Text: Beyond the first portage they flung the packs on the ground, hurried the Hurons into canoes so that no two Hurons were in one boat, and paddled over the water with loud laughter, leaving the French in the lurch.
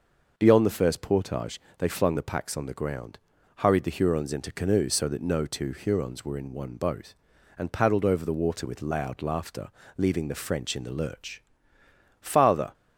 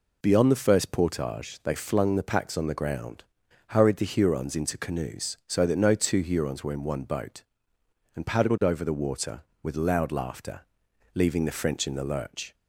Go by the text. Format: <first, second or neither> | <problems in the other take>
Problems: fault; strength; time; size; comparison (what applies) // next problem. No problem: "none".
second | pauses between "portage" and "they"; slight; at 1.5 s; 0.18 s long // goes on to say "Father"; from 12.1 s on; 0.54 s long